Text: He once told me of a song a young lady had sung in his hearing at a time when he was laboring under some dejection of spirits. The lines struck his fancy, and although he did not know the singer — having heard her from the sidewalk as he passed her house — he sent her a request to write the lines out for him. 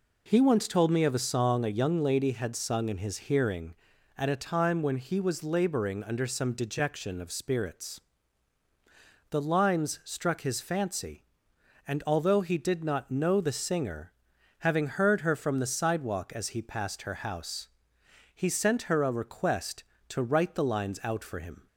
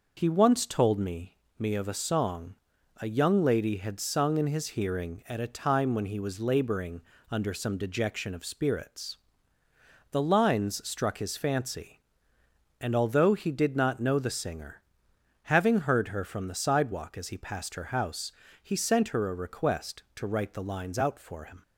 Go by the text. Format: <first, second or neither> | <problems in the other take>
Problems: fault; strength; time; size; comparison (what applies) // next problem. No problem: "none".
first | says "me" twice; at 1.5 s // pauses between "song" and "a"; at 2.5 s; 0.44 s long // pauses between "laboring" and "under"; slight; at 7.0 s; 0.28 s long